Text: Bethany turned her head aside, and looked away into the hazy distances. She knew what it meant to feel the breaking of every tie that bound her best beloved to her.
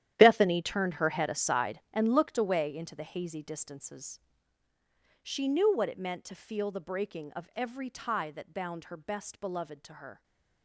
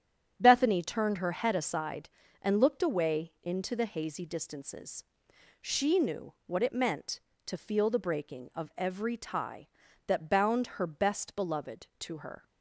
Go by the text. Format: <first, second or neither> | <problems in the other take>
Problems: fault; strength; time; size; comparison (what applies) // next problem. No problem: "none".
second | gets quieter; strong; throughout; 14.5 dB // starts louder than the rest; strong; until 1.1 s; 11.5 dB; strong in the second // stays silent after the last word; slight; from 10.1 s on; 0.5 s long